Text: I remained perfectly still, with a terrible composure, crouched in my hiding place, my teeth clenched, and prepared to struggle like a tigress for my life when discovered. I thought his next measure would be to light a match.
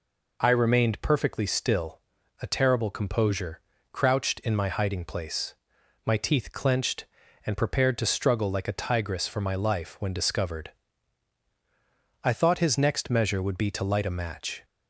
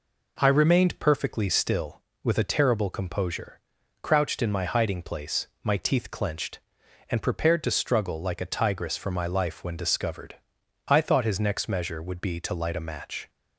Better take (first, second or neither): second